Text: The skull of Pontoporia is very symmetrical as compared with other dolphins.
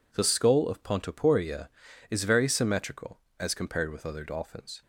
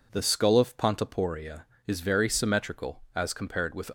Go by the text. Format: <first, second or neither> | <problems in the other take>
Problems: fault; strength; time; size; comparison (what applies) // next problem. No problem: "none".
first | stops before "other dolphins"; at 3.8 s